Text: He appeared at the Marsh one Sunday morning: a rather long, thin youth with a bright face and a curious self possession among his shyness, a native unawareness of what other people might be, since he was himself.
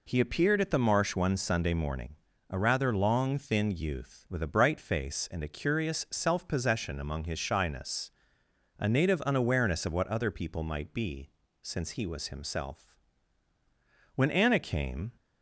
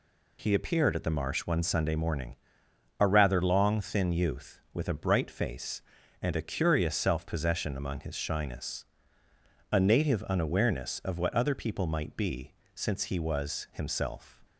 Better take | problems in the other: second | goes on to say "When Anna came"; noticeable; from 14.1 s on; 0.96 s long

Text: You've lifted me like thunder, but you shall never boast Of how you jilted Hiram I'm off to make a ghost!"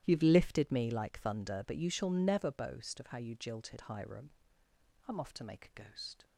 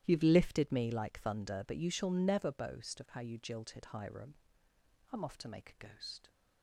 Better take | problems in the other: neither | starts louder than the rest; strong; the same in both // pauses between "Hiram" and "I'm"; noticeable; the same in both

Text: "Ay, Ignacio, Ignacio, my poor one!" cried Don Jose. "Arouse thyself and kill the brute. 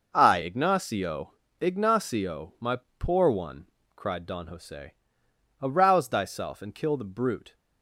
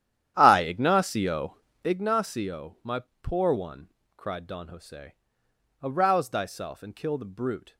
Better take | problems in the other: first | starts louder than the rest; strong; until 2.0 s; 10.5 dB // pauses between "my" and "poor"; slight; at 3.0 s; 0.18 s long; slight in the first

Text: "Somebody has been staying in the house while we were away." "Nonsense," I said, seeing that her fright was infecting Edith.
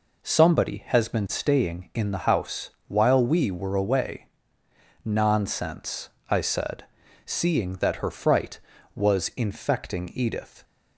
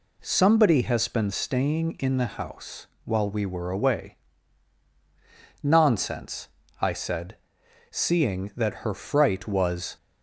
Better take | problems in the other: first | pauses between "house" and "while"; slight; at 2.8 s; 0.18 s long; slight in the first // stops before "infecting Edith"; at 9.9 s

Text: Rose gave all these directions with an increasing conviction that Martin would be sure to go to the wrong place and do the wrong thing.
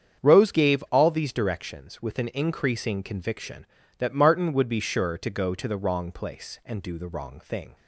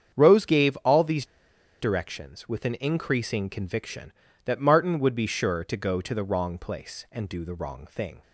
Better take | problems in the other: first | starts louder than the rest; strong; until 1.1 s; 8 dB; strong in the first // pauses between "these" and "directions"; noticeable; at 1.2 s; 0.55 s long

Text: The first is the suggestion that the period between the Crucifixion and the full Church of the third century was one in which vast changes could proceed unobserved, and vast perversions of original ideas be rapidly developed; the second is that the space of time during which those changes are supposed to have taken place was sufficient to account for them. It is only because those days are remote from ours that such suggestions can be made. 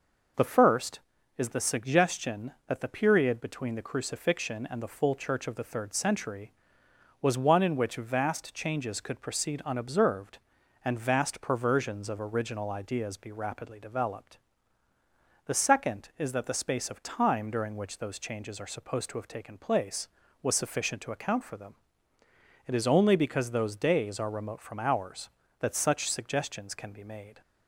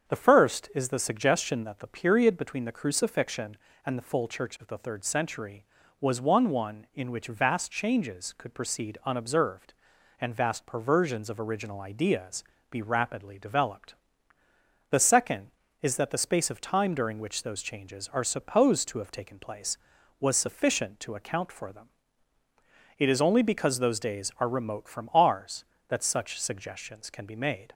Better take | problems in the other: first | starts louder than the rest; strong; until 1.1 s; 7.5 dB // says "one" twice; at 6.5 s // pauses between "ideas" and "be"; slight; at 12.4 s; 0.26 s long

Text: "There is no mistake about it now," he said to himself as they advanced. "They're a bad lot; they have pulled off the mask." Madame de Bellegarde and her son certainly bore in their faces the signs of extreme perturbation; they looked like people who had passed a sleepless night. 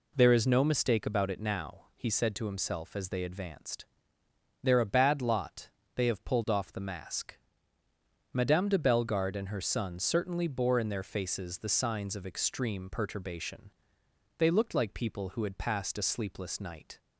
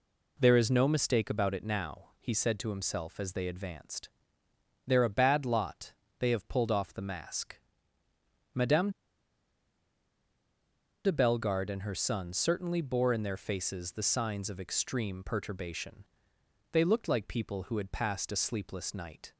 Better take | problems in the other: first | pauses between "Madame" and "de"; strong; at 8.8 s; 2.1 s long

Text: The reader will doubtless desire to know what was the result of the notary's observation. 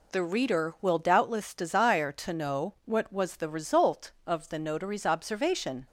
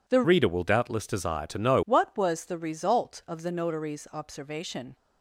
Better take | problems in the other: first | changes voice from "reader" to "know"; from 0.2 to 1.8 s; 1.6 s long

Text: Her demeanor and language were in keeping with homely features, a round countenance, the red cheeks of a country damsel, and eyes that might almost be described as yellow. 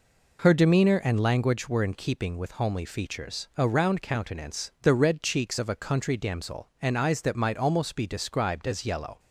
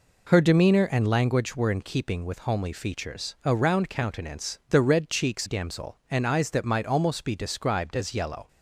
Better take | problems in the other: first | skips "of a country"; at 5.4 s

